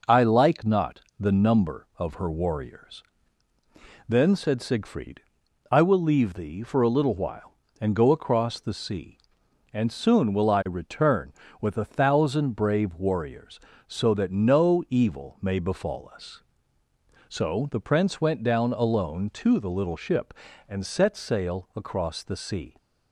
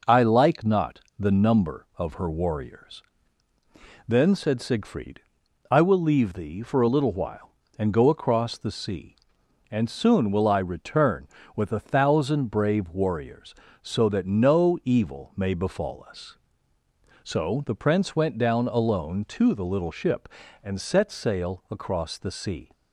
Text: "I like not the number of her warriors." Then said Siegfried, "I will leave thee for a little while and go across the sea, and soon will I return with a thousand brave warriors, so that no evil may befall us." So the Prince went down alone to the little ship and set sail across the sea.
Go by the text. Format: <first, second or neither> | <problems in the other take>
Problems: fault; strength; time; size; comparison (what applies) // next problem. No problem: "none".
neither | pauses between "not" and "the"; slight; the same in both